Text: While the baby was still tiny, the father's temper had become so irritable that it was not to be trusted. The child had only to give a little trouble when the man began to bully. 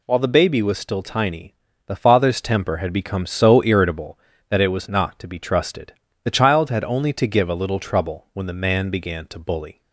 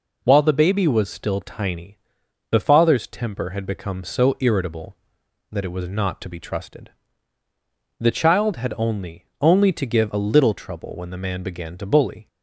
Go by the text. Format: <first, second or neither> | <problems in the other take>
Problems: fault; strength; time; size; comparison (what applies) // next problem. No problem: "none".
first | says "only" twice; at 9.4 s